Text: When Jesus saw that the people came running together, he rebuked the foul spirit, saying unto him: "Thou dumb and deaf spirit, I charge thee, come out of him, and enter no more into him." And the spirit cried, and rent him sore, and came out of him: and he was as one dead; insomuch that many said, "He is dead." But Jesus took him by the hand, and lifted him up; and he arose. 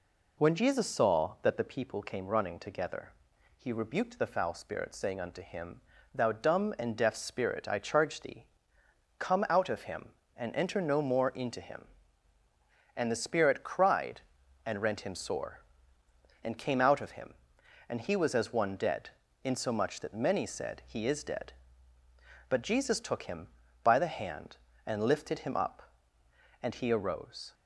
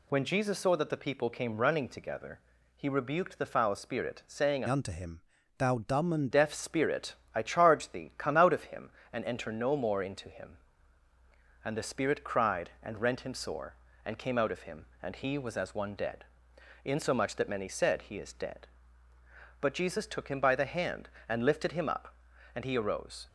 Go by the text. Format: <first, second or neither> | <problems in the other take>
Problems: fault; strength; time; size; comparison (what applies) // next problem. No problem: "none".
first | changes voice from "unto" to "and"; from 4.6 to 6.2 s; 1.6 s long